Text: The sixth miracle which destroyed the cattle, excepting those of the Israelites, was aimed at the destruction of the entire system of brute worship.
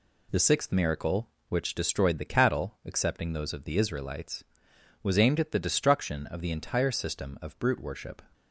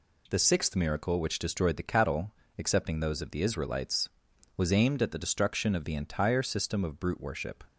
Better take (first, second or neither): neither